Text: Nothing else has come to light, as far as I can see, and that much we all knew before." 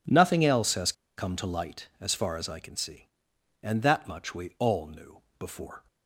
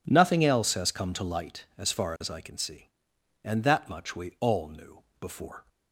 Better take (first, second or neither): second